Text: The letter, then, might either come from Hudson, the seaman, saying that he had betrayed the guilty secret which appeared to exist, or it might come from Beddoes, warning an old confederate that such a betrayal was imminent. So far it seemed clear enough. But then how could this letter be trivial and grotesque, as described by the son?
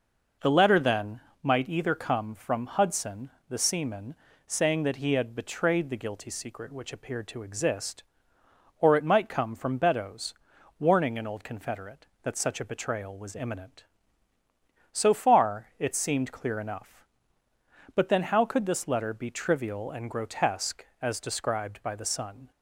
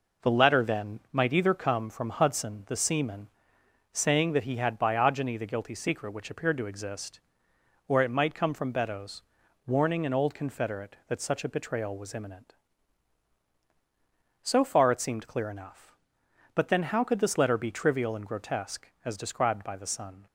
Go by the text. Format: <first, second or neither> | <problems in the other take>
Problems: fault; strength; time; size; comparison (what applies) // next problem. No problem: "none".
first | says "biogeny" for "betrayed"; at 4.7 s